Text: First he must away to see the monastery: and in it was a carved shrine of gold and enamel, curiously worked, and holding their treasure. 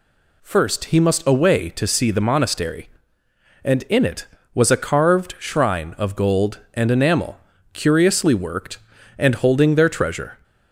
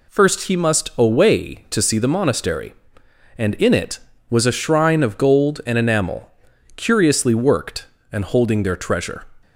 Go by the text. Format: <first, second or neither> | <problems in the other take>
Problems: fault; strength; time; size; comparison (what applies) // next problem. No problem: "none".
first | skips "carved"; at 4.5 s